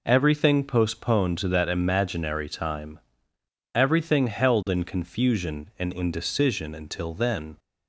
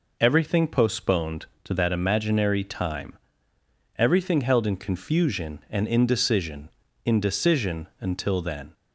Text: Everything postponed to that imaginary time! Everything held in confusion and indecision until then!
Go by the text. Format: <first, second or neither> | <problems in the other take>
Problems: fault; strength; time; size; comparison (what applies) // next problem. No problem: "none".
first | says "indecision" twice; at 7.0 s